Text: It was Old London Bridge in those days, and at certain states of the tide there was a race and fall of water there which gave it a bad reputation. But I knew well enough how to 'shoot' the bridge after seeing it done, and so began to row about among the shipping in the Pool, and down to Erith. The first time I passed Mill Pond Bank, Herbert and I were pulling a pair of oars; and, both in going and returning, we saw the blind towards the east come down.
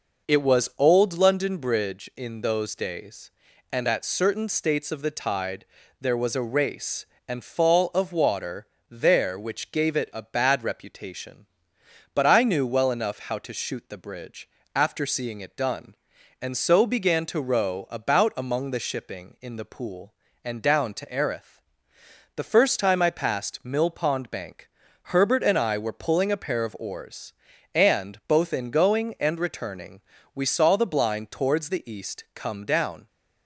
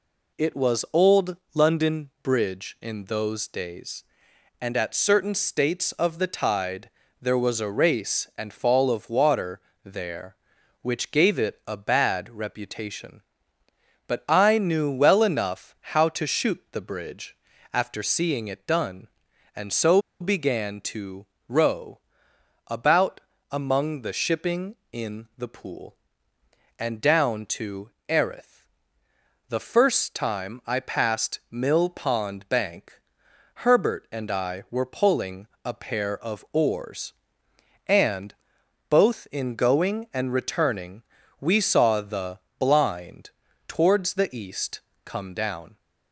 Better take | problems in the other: first | pauses between "Old" and "London"; slight; at 1.3 s; 0.18 s long // pauses between "tide" and "there"; slight; at 6.8 s; 0.32 s long; slight in the first // pauses between "water" and "there"; slight; at 9.5 s; 0.24 s long; slight in the first // pauses between "bridge" and "after"; slight; at 17.3 s; 0.34 s long; slight in the first // pauses between "so" and "began"; slight; at 20.0 s; 0.19 s long // pauses between "to" and "row"; slight; at 21.2 s; 0.24 s long // pauses between "row" and "about"; noticeable; at 21.9 s; 0.70 s long // pauses between "about" and "among"; slight; at 23.1 s; 0.32 s long // pauses between "to" and "Erith"; slight; at 27.9 s; 0.16 s long // pauses between "pulling" and "a"; slight; at 35.4 s; 0.16 s long // pauses between "the" and "blind"; slight; at 42.3 s; 0.18 s long // pauses between "blind" and "towards"; slight; at 43.3 s; 0.36 s long // pauses between "east" and "come"; slight; at 44.8 s; 0.24 s long

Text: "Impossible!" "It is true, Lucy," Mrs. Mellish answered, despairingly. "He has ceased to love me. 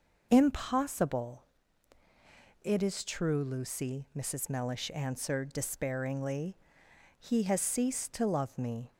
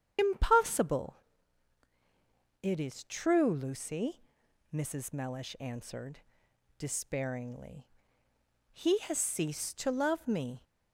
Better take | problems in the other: first | loses the start of "Impossible"; at 0.1 s; 95 ms // starts louder than the rest; strong; until 2.6 s; 8.5 dB

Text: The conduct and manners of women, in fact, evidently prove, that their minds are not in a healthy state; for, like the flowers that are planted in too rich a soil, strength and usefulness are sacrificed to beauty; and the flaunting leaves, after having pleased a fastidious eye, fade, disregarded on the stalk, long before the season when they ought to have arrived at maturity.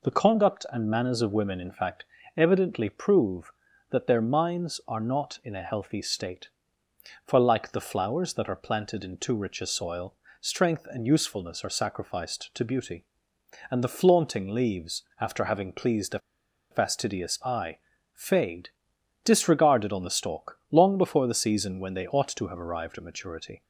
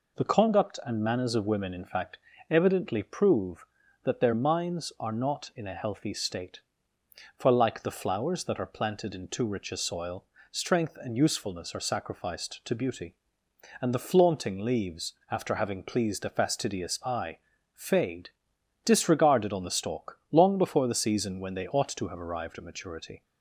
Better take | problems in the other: second | pauses between "a" and "fastidious"; noticeable; at 16.1 s; 0.51 s long

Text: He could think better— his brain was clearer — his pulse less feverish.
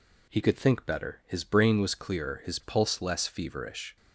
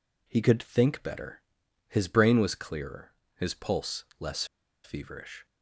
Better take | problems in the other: first | pauses between "less" and "feverish"; at 4.4 s; 0.39 s long

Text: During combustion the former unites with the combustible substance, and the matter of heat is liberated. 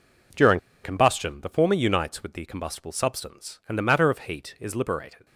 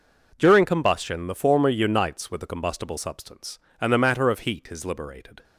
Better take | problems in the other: second | pauses between "During" and "combustion"; slight; at 0.5 s; 0.24 s long

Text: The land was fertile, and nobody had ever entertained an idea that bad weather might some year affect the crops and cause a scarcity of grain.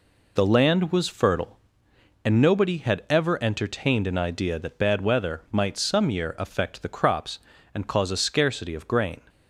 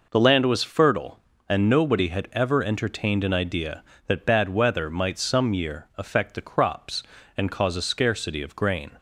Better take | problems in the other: neither | none

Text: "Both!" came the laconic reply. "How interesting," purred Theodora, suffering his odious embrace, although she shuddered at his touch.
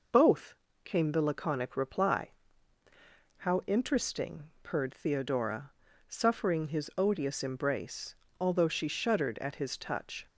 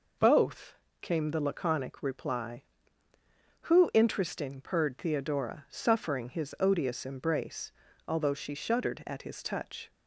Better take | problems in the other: first | says "Who" for "How"; at 3.6 s

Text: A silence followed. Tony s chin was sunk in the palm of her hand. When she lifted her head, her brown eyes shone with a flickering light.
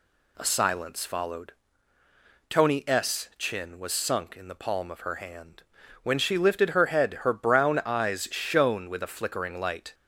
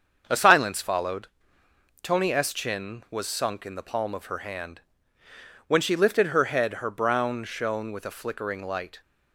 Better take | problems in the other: first | starts louder than the rest; until 1.2 s; 7 dB // skips "eyes"; at 7.4 s

